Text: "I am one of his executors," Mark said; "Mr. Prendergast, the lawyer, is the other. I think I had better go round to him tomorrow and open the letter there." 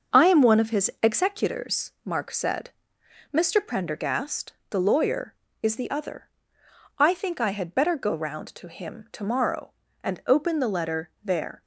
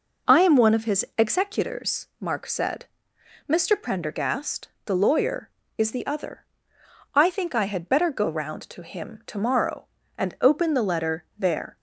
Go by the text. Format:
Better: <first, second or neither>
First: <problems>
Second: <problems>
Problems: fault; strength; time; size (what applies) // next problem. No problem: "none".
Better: second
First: gets quieter; noticeable; throughout; 5.5 dB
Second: none